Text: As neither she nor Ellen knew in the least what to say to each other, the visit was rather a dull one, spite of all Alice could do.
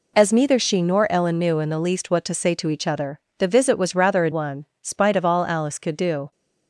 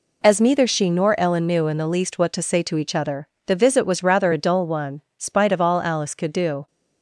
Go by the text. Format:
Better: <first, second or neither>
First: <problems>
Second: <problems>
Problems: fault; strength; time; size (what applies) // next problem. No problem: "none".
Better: second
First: skips "dull"; at 4.3 s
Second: none